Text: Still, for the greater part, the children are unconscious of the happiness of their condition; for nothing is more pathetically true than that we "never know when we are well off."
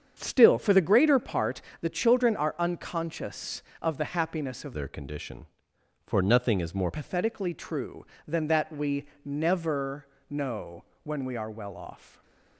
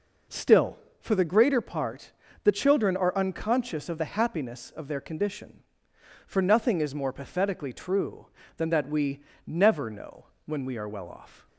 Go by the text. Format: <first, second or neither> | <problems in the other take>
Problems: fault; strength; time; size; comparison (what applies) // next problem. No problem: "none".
second | starts louder than the rest; strong; until 1.2 s; 7.5 dB // changes voice from "their" to "more"; from 4.7 to 6.9 s; 2.2 s long // pauses between "we" and "never"; slight; at 9.0 s; 0.18 s long; slight in the second // pauses between "never" and "know"; slight; at 10.0 s; 0.22 s long // pauses between "know" and "when"; slight; at 10.8 s; 0.20 s long; slight in the second // stays silent after the last word; slight; from 11.9 s on; 0.6 s long